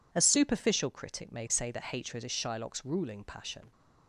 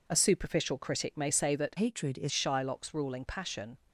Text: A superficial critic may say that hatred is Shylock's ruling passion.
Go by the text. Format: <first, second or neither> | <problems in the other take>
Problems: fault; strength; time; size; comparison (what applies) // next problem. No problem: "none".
first | changes voice from "hatred" to "is"; from 1.7 to 2.3 s; 0.6 s long